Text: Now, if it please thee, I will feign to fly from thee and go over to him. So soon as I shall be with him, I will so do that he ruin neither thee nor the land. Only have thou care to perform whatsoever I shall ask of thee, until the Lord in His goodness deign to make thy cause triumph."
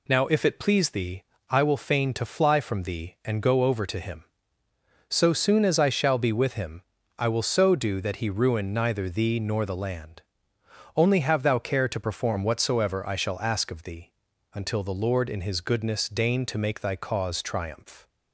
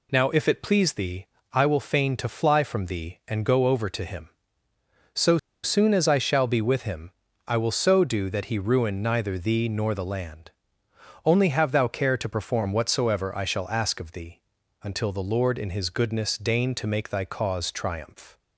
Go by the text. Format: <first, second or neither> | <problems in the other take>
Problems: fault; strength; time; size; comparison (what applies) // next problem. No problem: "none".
first | pauses between "So" and "soon"; slight; at 5.3 s; 0.26 s long